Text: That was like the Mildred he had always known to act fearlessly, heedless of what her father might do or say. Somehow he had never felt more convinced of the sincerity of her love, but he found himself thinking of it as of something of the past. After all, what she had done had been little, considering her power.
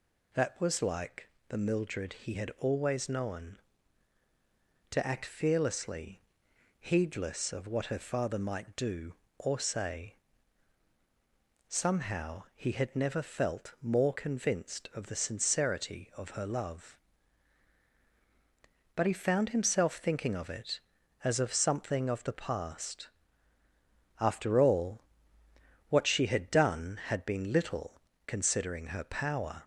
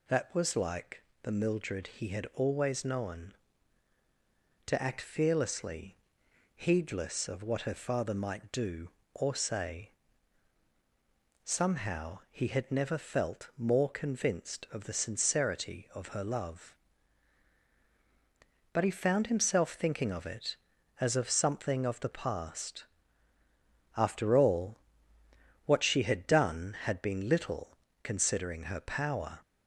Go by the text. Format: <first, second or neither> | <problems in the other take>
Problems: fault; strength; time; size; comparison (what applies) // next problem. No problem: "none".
neither | pauses between "like" and "the"; slight; the same in both